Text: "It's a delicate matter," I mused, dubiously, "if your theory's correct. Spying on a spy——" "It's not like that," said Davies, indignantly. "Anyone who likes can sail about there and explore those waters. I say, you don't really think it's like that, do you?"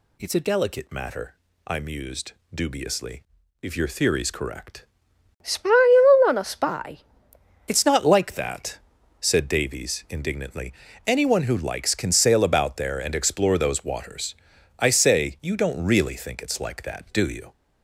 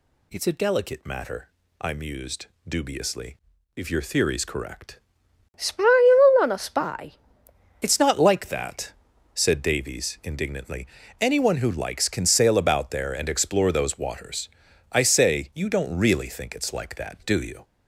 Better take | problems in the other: neither | none

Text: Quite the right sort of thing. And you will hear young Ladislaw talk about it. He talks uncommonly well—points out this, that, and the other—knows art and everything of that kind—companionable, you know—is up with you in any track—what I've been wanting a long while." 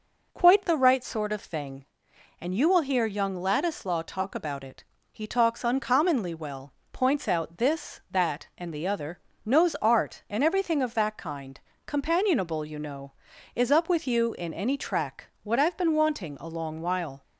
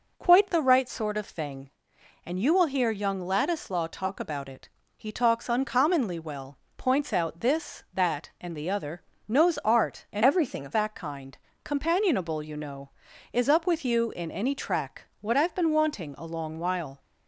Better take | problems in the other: first | changes voice from "everything" to "of"; from 10.2 to 10.7 s; 0.5 s long

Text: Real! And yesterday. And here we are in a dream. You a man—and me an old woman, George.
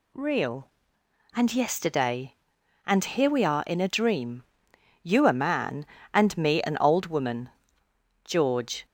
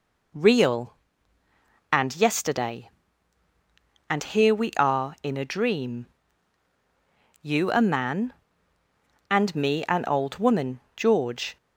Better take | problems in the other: neither | none

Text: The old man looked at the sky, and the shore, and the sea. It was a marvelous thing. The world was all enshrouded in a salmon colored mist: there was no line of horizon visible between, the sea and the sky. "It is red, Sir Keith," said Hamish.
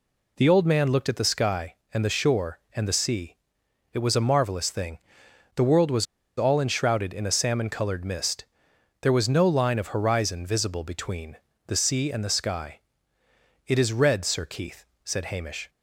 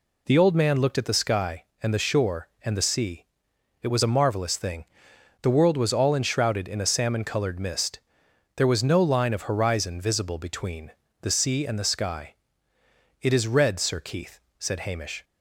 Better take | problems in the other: second | pauses between "was" and "all"; slight; at 6.0 s; 0.33 s long

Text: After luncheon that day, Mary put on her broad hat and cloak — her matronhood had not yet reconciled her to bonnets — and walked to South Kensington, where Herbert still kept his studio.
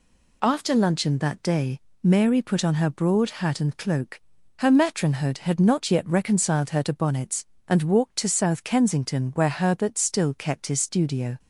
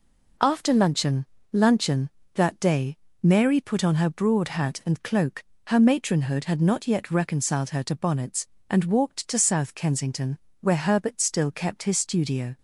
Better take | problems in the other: first | says "luncheon" twice; at 1.5 s

